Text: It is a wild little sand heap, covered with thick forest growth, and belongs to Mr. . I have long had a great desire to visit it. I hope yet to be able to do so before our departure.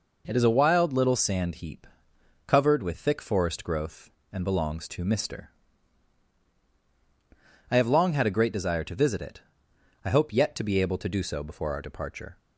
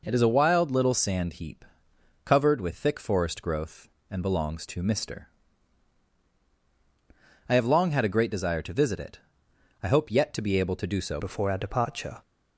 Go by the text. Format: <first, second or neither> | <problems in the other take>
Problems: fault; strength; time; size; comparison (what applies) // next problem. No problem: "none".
first | changes voice at "before"; from 11.1 s on; 1.1 s long